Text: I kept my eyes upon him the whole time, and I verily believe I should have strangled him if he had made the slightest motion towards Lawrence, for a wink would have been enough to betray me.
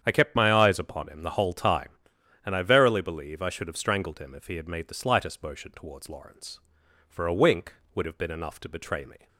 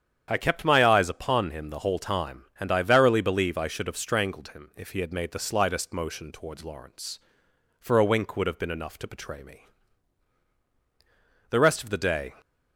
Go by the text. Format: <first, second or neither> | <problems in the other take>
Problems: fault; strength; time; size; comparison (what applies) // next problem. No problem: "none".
first | starts louder than the rest; strong; until 1.3 s; 8.5 dB; strong in the first // goes on to say "The rest of the day"; noticeable; from 11.4 s on; 0.86 s long